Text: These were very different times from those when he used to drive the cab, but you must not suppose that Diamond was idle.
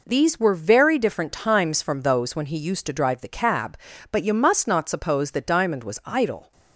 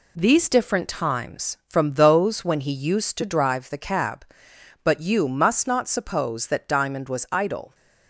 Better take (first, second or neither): first